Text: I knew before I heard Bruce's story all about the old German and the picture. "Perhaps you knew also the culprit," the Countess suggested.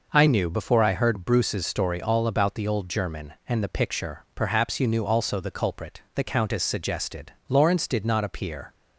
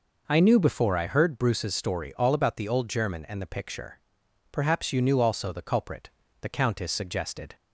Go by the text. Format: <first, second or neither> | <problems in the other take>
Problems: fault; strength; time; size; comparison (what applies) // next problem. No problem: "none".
second | goes on to say "Lawrence did not appear"; noticeable; from 7.4 s on; 1.2 s long